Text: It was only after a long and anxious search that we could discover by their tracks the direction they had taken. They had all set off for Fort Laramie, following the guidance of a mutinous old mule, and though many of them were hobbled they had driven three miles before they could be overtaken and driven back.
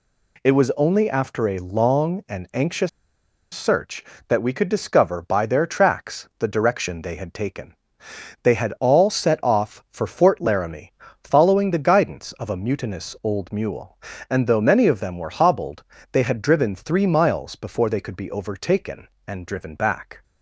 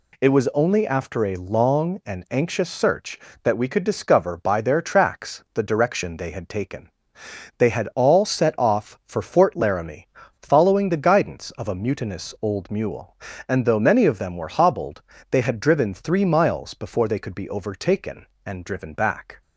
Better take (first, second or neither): second